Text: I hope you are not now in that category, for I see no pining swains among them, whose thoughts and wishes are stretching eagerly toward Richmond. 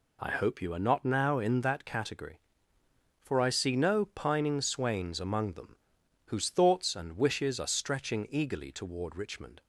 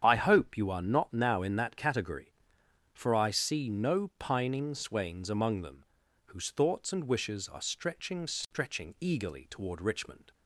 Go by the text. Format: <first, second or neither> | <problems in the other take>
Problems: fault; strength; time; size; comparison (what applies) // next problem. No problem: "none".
first | starts louder than the rest; strong; until 1.0 s; 8 dB // says "stretching" twice; at 8.2 s